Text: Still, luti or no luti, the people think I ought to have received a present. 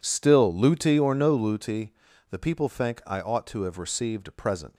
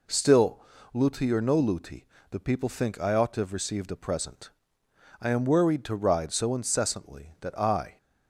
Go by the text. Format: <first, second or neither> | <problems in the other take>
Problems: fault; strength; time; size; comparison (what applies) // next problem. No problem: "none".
first | goes on to say "I am worried to ride so incessantly that I"; strong; from 5.2 s on; 2.7 s long